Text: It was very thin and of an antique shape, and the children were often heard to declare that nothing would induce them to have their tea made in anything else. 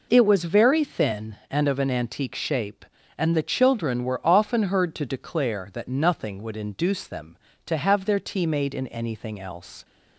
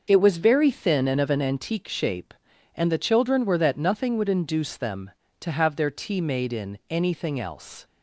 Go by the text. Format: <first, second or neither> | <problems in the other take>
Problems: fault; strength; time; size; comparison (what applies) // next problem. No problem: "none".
first | starts louder than the rest; noticeable; until 1.0 s; 6 dB // skips "often heard to declare"; at 3.5 s